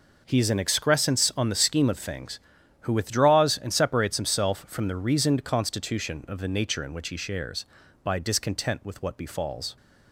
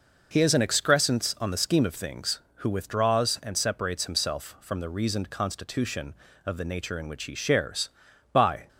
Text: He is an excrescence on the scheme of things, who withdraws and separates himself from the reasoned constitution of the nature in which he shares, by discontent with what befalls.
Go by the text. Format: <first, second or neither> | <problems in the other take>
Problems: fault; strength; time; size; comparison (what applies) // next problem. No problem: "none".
first | stops before "discontent with what befalls"; at 8.6 s